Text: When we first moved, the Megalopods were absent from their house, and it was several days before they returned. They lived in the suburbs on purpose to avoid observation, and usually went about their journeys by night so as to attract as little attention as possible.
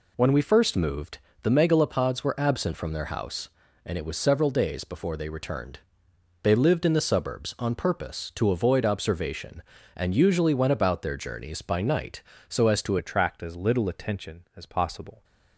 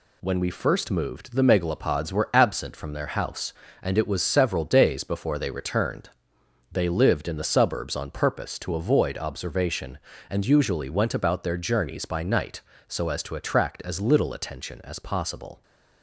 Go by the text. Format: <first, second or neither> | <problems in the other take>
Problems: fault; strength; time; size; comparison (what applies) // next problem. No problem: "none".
second | changes voice at "attract"; from 12.9 s on; 2.3 s long